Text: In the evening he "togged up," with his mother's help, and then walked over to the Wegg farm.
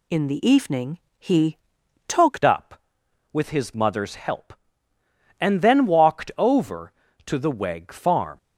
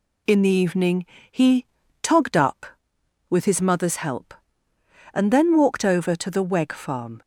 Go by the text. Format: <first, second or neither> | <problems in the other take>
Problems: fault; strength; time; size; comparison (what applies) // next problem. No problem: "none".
second | pauses between "evening" and "he"; slight; at 0.9 s; 0.20 s long; slight in the second // pauses between "he" and "togged"; noticeable; at 1.5 s; 0.50 s long; slight in the second // changes voice at "up"; from 2.4 s on; 5.9 s long